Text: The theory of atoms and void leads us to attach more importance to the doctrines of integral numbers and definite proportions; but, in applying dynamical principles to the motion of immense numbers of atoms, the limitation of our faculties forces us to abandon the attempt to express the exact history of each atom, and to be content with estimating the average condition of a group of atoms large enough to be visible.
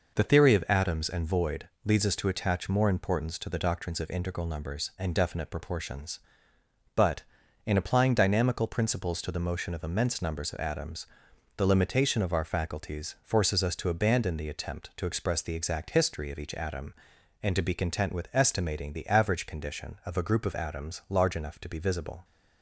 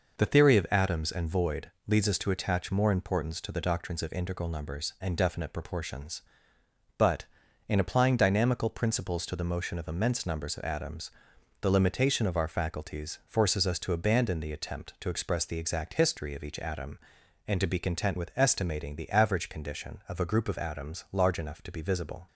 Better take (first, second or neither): neither